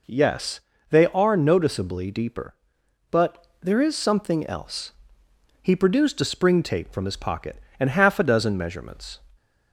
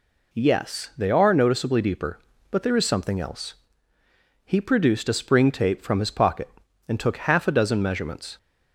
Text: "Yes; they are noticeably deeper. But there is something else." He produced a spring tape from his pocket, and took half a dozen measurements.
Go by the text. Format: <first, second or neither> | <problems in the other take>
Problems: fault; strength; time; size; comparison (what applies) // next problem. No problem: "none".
second | skips "took"; at 7.8 s